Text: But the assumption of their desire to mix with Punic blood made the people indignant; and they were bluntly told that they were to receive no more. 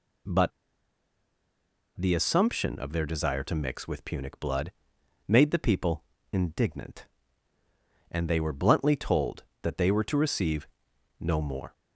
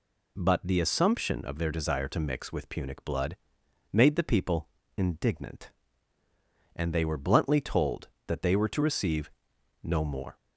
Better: second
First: pauses between "But" and "the"; strong; at 0.5 s; 1.4 s long // pauses between "blood" and "made"; noticeable; at 4.7 s; 0.56 s long // pauses between "people" and "indignant"; slight; at 6.0 s; 0.30 s long // pauses between "receive" and "no"; noticeable; at 10.6 s; 0.54 s long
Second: pauses between "blood" and "made"; noticeable; at 3.3 s; 0.56 s long // pauses between "people" and "indignant"; slight; at 4.6 s; 0.30 s long // pauses between "receive" and "no"; noticeable; at 9.2 s; 0.54 s long

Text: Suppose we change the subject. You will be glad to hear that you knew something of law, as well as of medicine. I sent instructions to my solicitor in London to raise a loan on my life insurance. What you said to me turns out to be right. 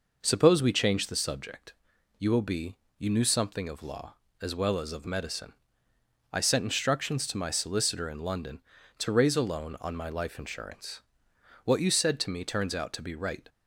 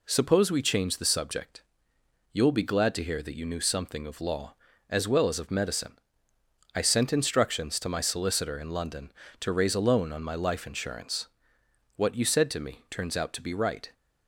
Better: second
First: skips "glad to hear that"; at 2.8 s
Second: none

